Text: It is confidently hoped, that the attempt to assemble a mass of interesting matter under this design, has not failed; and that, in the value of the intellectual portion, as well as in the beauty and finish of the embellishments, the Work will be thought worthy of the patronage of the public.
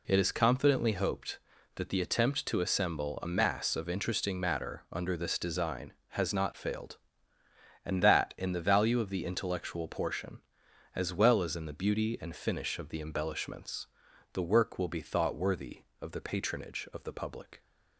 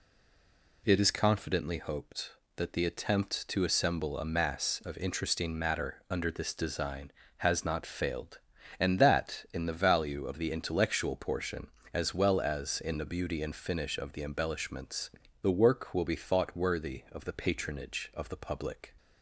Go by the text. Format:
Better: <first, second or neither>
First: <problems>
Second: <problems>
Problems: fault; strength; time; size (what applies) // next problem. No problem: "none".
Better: first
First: none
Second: stays silent before the first word; slight; until 0.8 s; 0.8 s long